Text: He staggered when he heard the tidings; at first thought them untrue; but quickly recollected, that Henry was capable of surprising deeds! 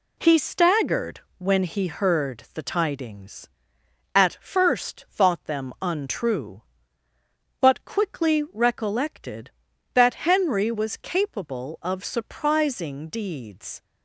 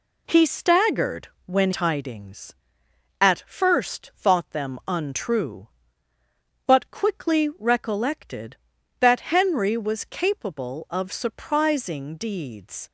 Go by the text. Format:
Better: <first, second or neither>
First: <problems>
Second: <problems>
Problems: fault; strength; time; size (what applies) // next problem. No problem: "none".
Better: first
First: pauses between "staggered" and "when"; slight; at 1.2 s; 0.18 s long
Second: pauses between "staggered" and "when"; slight; at 1.2 s; 0.18 s long // skips "he heard the"; at 1.7 s